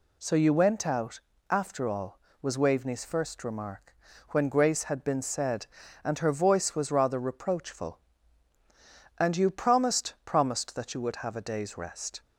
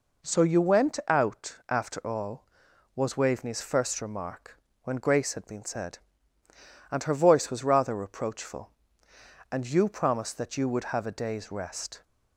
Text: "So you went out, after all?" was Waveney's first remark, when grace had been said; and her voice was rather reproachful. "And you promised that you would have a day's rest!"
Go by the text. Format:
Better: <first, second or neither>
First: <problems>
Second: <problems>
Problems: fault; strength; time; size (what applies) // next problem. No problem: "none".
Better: second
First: says "promised" twice; at 10.2 s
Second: none